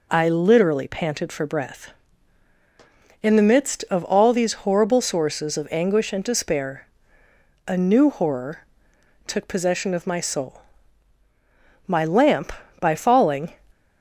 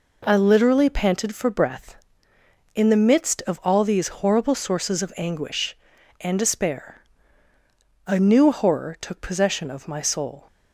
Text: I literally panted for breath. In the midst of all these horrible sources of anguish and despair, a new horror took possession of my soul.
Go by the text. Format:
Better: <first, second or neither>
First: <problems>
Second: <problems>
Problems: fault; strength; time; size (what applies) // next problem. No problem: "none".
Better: second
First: pauses between "horror" and "took"; noticeable; at 8.6 s; 0.62 s long // goes on to say "My lamp by falling"; from 11.8 s on; 1.6 s long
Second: none